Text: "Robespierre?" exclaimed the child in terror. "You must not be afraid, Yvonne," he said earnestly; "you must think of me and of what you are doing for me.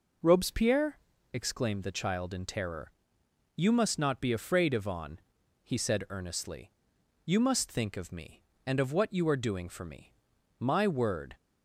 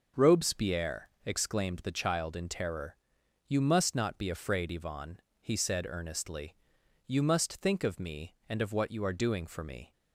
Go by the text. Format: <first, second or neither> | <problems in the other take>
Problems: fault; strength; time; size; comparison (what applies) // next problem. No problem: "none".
second | goes on to say "My word"; noticeable; from 10.5 s on; 0.78 s long